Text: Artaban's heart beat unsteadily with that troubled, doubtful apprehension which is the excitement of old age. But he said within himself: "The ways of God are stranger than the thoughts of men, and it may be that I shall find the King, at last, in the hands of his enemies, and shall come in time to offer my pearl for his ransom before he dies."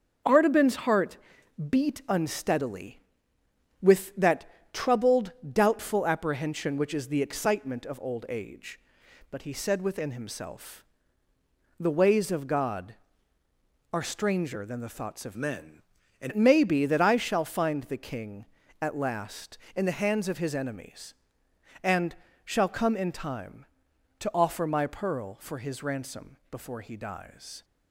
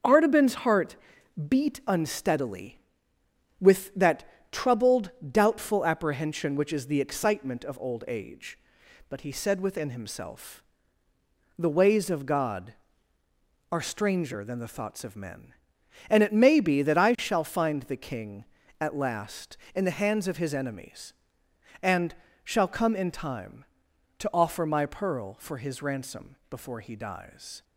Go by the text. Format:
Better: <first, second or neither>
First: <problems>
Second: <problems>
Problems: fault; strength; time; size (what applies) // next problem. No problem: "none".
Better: second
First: starts louder than the rest; until 1.7 s; 6.5 dB // pauses between "heart" and "beat"; noticeable; at 1.1 s; 0.52 s long // pauses between "that" and "troubled"; slight; at 4.4 s; 0.26 s long // changes voice from "men" to "and"; from 15.3 to 16.3 s; 1.0 s long // pauses between "and" and "shall"; slight; at 22.1 s; 0.30 s long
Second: starts louder than the rest; until 1.5 s; 6.5 dB // pauses between "heart" and "beat"; noticeable; at 0.9 s; 0.52 s long // pauses between "that" and "troubled"; slight; at 4.2 s; 0.26 s long // pauses between "and" and "shall"; slight; at 22.1 s; 0.30 s long